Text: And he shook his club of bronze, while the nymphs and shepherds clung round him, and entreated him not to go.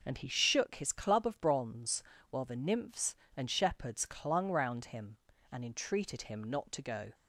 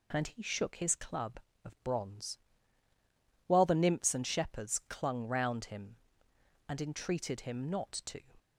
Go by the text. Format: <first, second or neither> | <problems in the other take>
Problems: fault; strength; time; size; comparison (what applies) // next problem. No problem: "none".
first | stops before "go"; at 8.3 s